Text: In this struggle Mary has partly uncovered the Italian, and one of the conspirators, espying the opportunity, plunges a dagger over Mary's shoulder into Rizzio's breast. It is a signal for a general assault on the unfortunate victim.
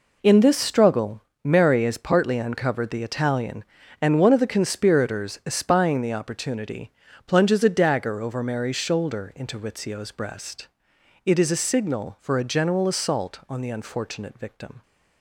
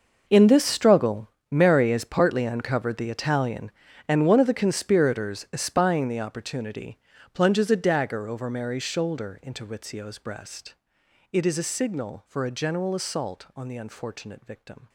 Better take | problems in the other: first | gets quieter; strong; throughout; 16.5 dB // pauses between "struggle" and "Mary"; slight; at 1.2 s; 0.24 s long; slight in the first

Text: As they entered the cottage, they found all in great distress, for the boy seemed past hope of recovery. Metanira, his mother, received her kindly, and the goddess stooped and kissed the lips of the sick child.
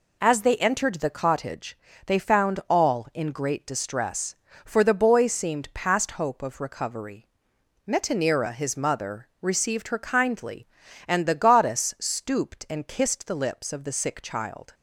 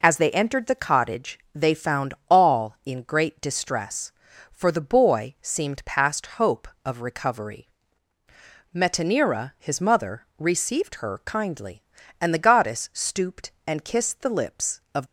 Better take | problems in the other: first | stops before "the sick child"; at 15.0 s

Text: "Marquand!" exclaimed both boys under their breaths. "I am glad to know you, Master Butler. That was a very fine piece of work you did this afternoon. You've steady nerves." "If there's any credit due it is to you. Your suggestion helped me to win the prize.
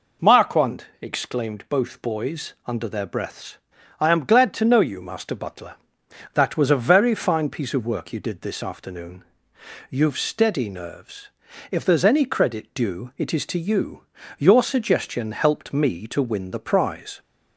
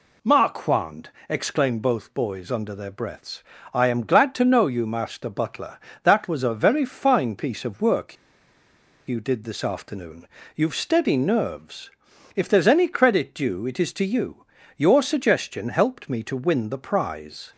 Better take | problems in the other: first | pauses between "work" and "you"; noticeable; at 8.1 s; 0.93 s long

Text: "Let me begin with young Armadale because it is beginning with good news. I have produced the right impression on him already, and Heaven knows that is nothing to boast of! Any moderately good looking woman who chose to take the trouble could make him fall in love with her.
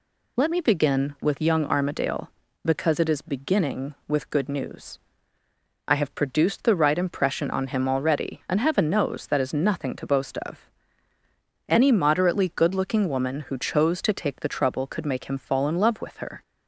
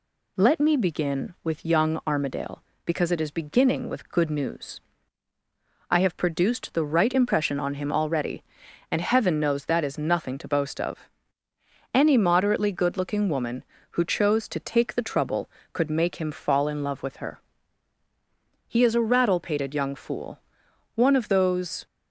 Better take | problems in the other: first | goes on to say "He is a rattle pated young fool one of those"; strong; from 18.6 s on; 3.1 s long

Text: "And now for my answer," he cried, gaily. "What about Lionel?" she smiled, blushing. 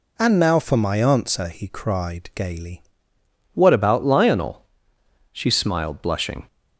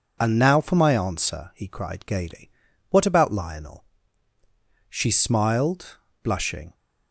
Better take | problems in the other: second | changes voice at "What"; from 3.5 s on; 2.9 s long

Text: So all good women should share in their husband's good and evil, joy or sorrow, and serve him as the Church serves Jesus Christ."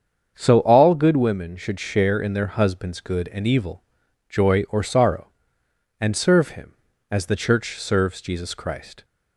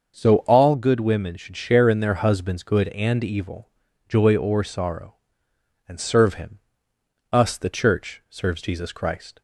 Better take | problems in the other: first | starts louder than the rest; until 1.2 s; 6.5 dB; strong in the first // says "us" for "as"; at 7.3 s

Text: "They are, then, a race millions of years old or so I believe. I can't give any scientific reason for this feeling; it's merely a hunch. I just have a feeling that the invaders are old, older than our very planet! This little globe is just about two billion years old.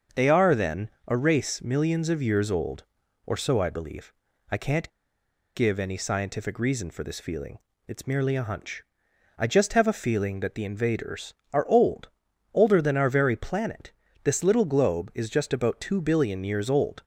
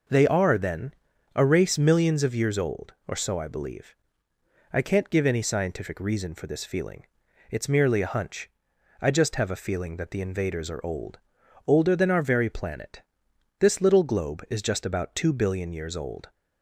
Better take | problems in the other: second | starts louder than the rest; until 1.3 s; 6.5 dB // pauses between "can't" and "give"; noticeable; at 4.9 s; 0.64 s long

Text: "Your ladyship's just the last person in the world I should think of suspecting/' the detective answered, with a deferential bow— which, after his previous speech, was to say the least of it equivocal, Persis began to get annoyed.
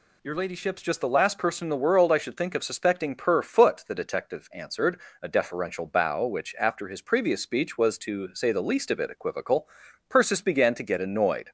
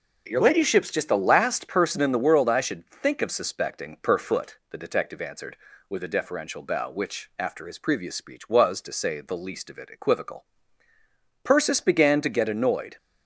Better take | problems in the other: second | skips "with"; at 5.1 s

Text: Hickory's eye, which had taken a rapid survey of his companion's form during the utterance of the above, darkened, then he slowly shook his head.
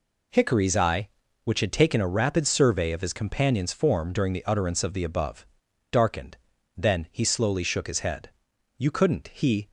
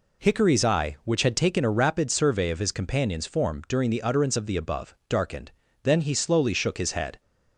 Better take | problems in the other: second | goes on to say "You couldn't he"; noticeable; from 8.7 s on; 0.94 s long

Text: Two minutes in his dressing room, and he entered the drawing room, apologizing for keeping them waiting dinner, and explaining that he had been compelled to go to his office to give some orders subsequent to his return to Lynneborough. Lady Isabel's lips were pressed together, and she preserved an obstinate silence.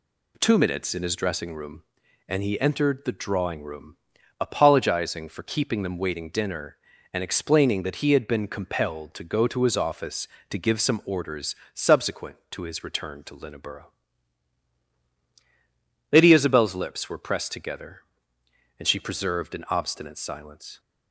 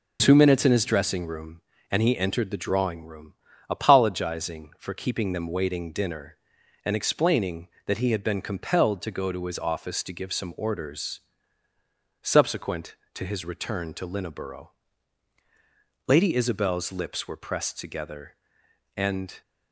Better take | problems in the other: first | pauses between "orders" and "subsequent"; at 11.2 s; 1.0 s long; slight in the first // stops before "she preserved an obstinate silence"; at 19.4 s

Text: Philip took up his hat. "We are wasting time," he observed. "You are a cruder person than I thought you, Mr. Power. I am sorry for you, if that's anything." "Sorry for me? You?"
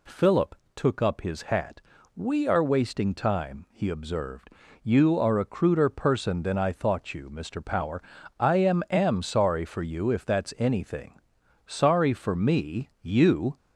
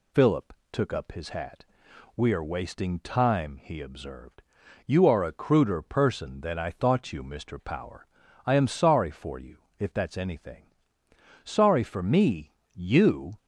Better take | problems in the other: second | pauses between "Philip" and "took"; slight; at 0.5 s; 0.22 s long; slight in the second // says "am" twice; at 8.8 s

